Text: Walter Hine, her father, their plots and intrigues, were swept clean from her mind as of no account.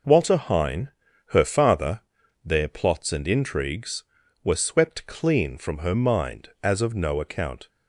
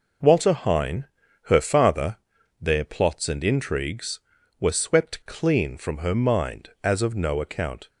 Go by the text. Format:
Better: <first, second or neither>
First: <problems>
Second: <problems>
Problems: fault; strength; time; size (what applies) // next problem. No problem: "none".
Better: neither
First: none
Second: none